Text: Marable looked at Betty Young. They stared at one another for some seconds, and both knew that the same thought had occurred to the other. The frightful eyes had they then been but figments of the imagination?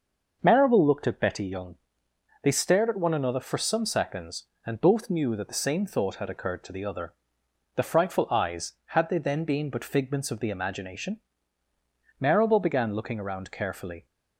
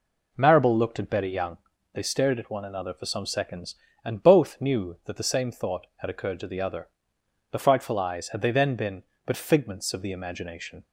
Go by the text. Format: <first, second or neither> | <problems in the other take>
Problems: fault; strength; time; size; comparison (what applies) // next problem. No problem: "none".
second | starts louder than the rest; noticeable; until 1.4 s; 6 dB // goes on to say "Marable began looking around carefully"; strong; from 12.1 s on; 1.8 s long